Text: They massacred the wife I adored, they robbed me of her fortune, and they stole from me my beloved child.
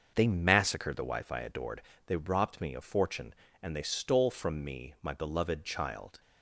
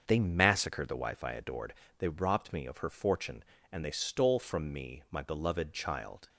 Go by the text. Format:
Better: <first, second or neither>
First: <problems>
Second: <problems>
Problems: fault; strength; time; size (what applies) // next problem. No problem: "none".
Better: second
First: starts louder than the rest; until 1.1 s; 6.5 dB // skips "her"; at 2.8 s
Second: starts louder than the rest; until 1.0 s; 6.5 dB